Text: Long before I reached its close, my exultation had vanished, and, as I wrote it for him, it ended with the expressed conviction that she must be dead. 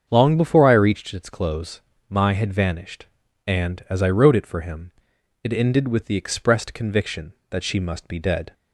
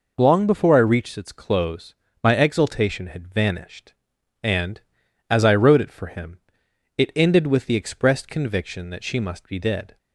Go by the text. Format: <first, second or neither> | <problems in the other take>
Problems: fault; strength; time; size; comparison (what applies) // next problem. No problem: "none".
second | starts louder than the rest; strong; until 1.1 s; 7.5 dB // skips "exultation"; at 2.3 s